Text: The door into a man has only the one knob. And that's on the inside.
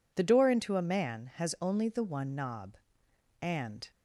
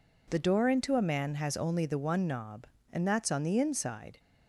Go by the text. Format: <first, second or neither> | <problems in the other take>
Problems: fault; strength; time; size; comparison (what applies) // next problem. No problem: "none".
second | stops before "that's on the inside"; at 3.9 s